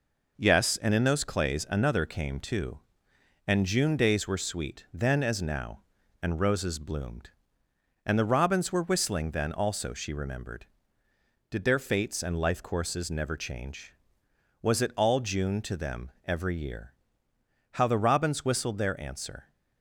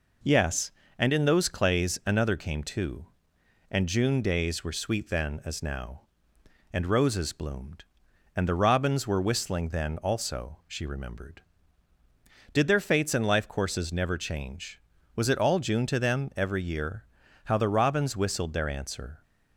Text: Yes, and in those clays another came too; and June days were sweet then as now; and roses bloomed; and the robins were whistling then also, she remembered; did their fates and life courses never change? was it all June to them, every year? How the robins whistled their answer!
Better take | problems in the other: neither | none

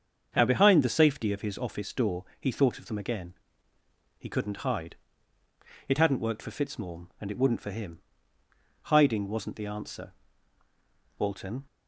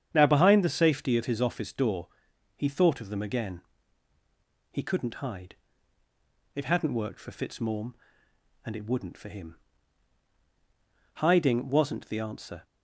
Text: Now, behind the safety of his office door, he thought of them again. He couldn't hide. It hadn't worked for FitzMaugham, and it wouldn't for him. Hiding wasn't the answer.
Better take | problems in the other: second | starts louder than the rest; until 1.3 s; 7 dB; strong in the second // goes on to say "Walton"; slight; from 11.1 s on; 0.46 s long

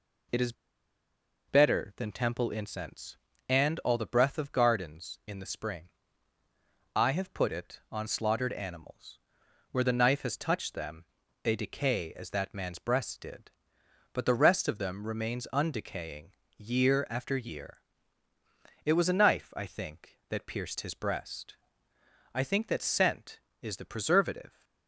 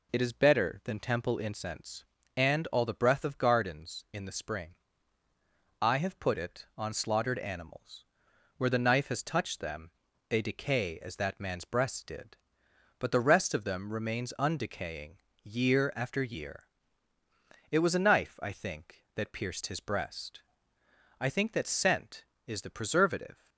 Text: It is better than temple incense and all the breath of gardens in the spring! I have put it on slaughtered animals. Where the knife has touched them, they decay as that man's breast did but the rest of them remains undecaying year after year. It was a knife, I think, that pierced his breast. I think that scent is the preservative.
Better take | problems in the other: second | pauses between "is" and "better"; noticeable; at 0.5 s; 0.95 s long // pauses between "undecaying" and "year"; slight; at 16.3 s; 0.26 s long; slight in the second

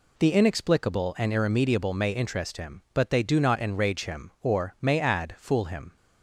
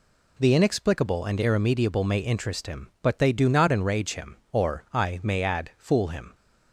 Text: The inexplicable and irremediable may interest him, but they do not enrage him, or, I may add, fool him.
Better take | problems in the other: second | skips "I"; at 4.7 s

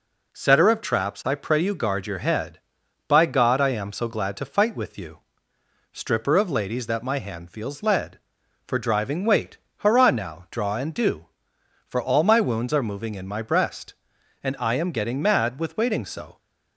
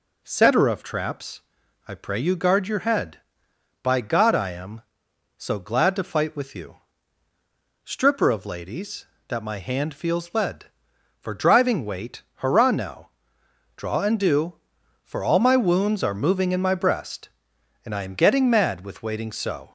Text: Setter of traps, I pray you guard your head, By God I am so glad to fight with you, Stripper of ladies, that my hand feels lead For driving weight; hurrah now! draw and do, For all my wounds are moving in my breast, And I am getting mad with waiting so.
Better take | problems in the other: neither | none

